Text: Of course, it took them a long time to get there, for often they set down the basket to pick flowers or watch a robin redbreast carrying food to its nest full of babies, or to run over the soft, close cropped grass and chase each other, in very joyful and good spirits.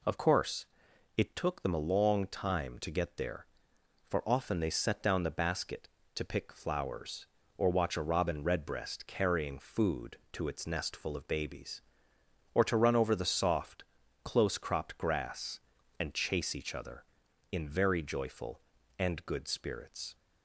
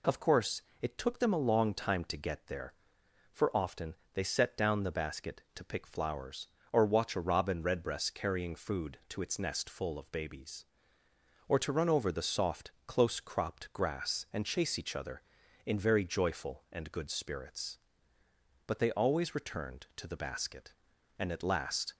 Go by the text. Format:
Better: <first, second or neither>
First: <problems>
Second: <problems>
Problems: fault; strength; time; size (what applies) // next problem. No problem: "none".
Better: first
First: none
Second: pauses between "often" and "they"; slight; at 3.9 s; 0.18 s long // goes on to say "But they always returned to the basket and at last"; strong; from 18.6 s on; 3.2 s long